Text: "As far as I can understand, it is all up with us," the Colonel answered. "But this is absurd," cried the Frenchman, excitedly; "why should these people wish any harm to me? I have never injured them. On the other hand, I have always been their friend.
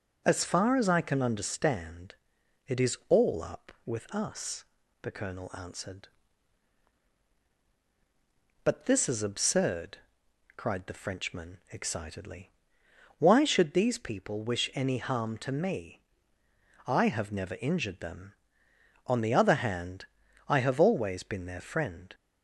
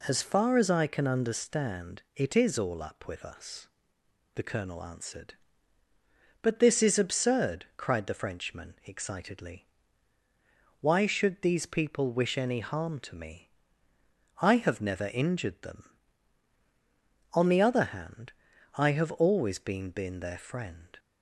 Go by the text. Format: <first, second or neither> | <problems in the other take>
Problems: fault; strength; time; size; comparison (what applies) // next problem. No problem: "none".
first | says "been" twice; at 19.9 s